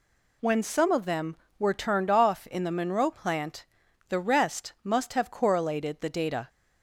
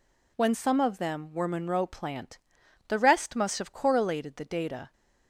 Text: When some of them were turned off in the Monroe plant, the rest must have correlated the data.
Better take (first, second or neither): first